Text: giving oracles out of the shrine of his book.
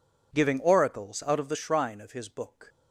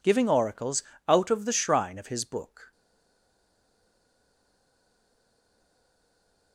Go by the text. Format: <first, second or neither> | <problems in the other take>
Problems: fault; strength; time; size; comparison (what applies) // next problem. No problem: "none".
first | pauses between "oracles" and "out"; slight; at 0.8 s; 0.24 s long // stays silent after the last word; strong; from 2.7 s on; 3.8 s long